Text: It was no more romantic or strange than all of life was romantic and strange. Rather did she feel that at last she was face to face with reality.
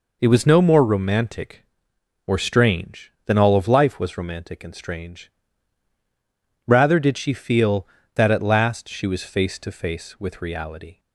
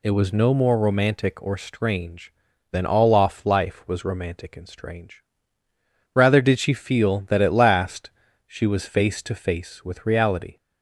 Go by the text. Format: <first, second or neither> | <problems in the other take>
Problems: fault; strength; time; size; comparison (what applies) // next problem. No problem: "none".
first | says "off" for "of"; at 3.1 s // pauses between "last" and "she"; slight; at 8.1 s; 0.36 s long